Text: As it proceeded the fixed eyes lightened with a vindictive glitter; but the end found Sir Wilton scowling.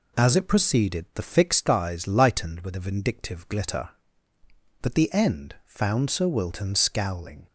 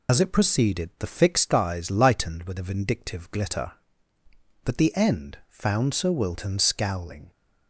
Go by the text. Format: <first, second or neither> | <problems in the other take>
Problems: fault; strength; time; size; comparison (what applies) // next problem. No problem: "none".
first | loses the start of "As"; at 0.0 s; 95 ms